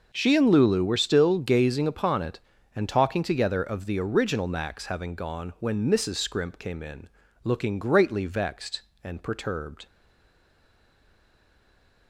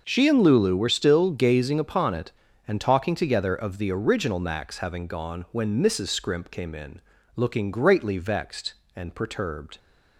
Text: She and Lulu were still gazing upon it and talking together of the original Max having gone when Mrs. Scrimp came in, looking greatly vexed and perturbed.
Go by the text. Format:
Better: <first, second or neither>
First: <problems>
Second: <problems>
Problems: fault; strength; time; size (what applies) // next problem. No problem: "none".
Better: second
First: stays silent after the last word; from 9.8 s on; 2.2 s long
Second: none